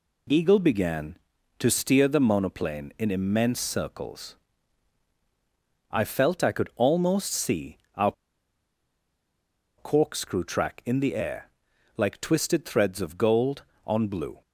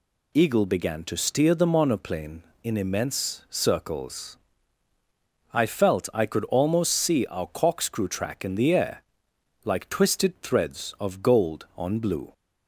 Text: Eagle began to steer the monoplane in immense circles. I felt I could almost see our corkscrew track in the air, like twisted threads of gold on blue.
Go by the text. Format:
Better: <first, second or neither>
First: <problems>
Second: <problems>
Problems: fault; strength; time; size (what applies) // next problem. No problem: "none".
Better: second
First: pauses between "see" and "our"; slight; at 7.7 s; 0.18 s long // pauses between "our" and "corkscrew"; strong; at 8.1 s; 1.6 s long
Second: none